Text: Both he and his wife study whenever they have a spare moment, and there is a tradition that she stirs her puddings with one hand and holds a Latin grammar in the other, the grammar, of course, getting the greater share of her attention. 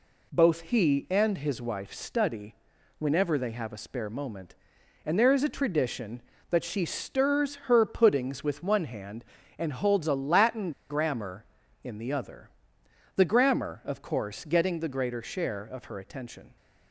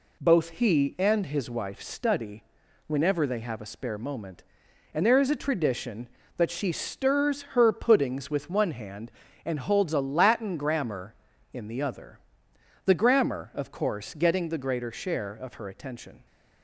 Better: second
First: pauses between "study" and "whenever"; at 2.5 s; 0.44 s long // pauses between "Latin" and "grammar"; slight; at 10.7 s; 0.18 s long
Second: pauses between "study" and "whenever"; at 2.4 s; 0.44 s long

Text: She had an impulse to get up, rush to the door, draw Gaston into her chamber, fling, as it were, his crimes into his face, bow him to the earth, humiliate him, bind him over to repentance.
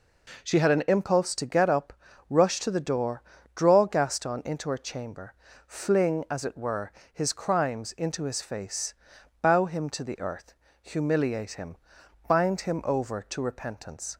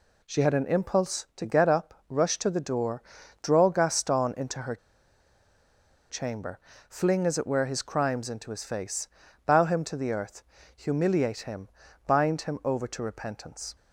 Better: first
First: none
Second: pauses between "her" and "chamber"; strong; at 4.7 s; 1.3 s long

